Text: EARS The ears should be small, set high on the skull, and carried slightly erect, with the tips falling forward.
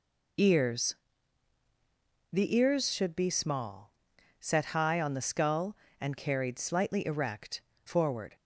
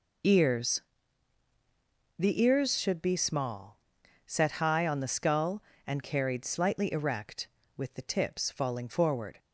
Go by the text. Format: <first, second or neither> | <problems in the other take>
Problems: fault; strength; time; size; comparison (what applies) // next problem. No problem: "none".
second | pauses between "EARS" and "The"; strong; at 0.9 s; 1.3 s long; strong in the second // skips "with the tips falling"; at 7.7 s